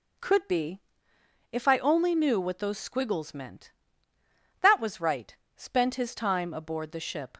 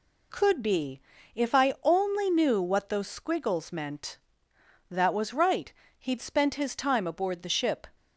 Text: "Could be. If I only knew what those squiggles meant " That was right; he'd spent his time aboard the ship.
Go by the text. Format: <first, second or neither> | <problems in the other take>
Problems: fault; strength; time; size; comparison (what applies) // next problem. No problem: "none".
second | skips "he'd"; at 5.4 s